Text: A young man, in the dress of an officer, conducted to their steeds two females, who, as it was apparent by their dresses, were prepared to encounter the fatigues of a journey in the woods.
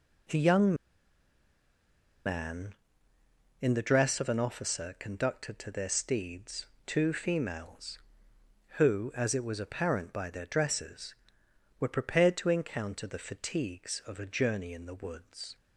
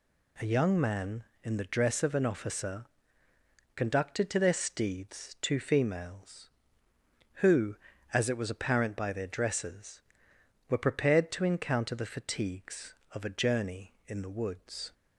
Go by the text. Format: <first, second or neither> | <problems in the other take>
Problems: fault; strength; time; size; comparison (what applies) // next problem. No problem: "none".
second | pauses between "young" and "man"; strong; at 0.7 s; 1.5 s long // pauses between "steeds" and "two"; slight; at 6.6 s; 0.20 s long